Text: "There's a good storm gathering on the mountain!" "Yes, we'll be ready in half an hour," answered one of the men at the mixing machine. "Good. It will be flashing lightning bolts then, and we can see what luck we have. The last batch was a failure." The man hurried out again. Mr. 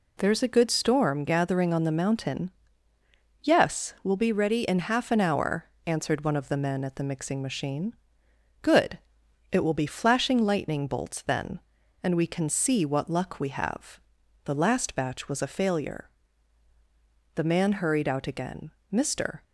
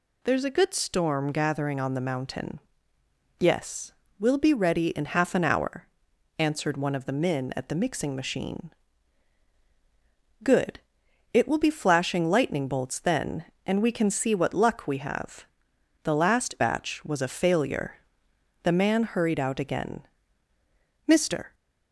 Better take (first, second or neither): neither